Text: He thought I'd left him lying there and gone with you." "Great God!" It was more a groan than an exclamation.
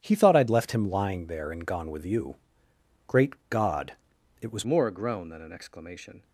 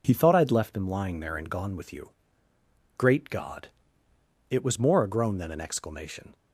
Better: second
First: pauses between "Great" and "God"; slight; at 3.3 s; 0.16 s long // changes voice at "more"; from 4.6 s on; 1.6 s long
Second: none

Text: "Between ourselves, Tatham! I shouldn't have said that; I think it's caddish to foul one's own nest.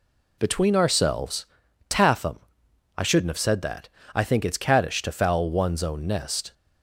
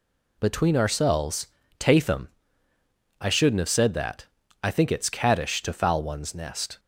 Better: first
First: none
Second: skips "own"; at 6.3 s

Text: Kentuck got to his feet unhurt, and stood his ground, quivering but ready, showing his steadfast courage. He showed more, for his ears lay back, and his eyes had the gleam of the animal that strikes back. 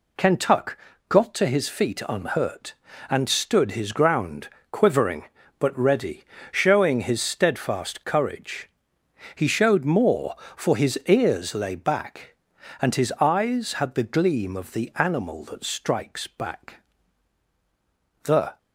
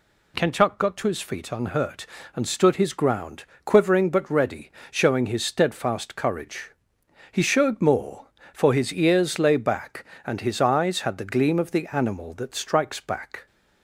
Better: second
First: pauses between "Kentuck" and "got"; slight; at 0.7 s; 0.32 s long // goes on to say "The"; slight; from 18.2 s on; 0.34 s long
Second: none

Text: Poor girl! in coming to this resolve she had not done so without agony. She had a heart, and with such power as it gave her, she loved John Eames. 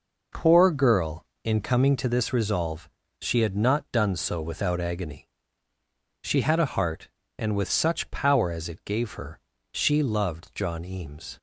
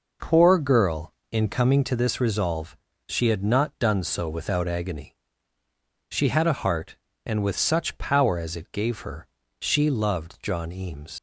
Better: first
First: pauses between "resolve" and "she"; slight; at 2.8 s; 0.32 s long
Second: pauses between "resolve" and "she"; slight; at 2.7 s; 0.32 s long // leaves "Eames" unfinished; at 11.1 s; 65 ms

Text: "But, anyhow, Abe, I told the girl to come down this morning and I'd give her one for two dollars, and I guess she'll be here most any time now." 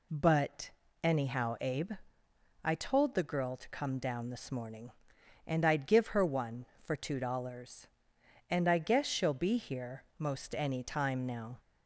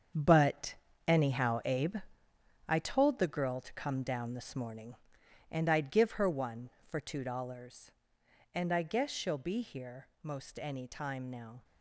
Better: first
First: pauses between "here" and "most"; slight; at 10.0 s; 0.16 s long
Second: gets quieter; strong; throughout; 10 dB // pauses between "here" and "most"; slight; at 10.0 s; 0.16 s long

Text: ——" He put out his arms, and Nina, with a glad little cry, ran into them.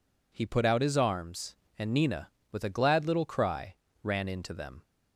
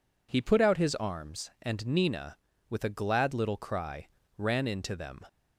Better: neither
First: none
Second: none

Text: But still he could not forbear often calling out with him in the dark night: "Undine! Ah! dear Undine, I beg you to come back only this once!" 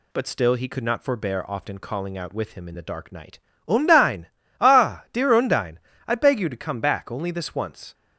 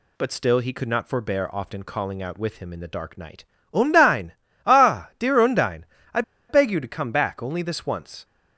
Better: first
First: none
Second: pauses between "I" and "beg"; slight; at 6.2 s; 0.27 s long

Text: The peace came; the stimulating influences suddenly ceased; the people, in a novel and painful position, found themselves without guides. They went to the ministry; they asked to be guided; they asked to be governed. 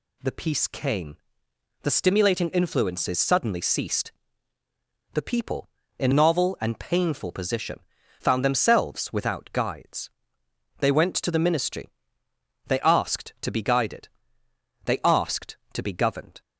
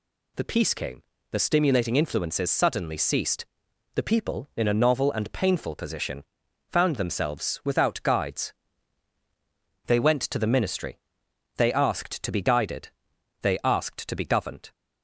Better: second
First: skips "a"; at 6.1 s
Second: none

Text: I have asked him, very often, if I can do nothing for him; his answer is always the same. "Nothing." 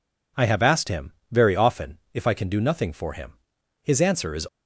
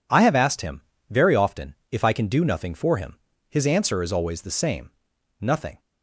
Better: second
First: stops before "always the same Nothing"; at 4.4 s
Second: none

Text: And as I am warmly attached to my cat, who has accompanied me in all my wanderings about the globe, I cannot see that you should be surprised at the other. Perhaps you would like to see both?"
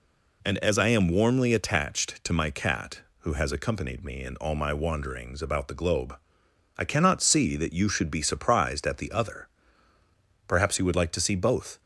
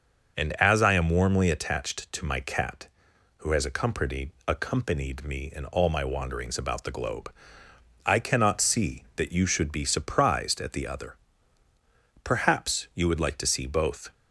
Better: first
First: none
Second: starts louder than the rest; until 1.4 s; 6 dB // says "accompanied" twice; at 4.4 s

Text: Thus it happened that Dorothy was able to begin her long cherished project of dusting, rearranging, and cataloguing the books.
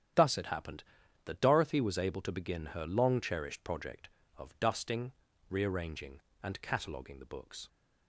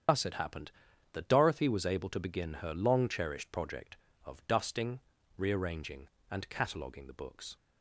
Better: first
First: starts louder than the rest; strong; until 1.5 s; 9.5 dB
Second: loses the start of "Thus"; at 0.0 s; 50 ms // starts louder than the rest; strong; until 1.5 s; 8 dB

